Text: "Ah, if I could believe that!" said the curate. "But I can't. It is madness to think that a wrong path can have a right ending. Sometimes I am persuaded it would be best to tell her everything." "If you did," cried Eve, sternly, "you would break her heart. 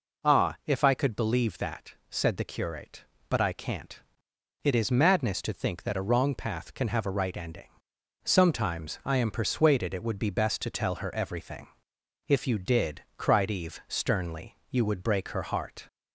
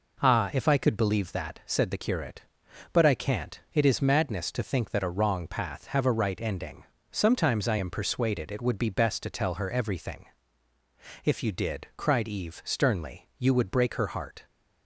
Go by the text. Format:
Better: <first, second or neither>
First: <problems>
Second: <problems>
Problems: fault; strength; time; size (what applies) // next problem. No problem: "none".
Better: first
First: none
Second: skips "can"; at 5.8 s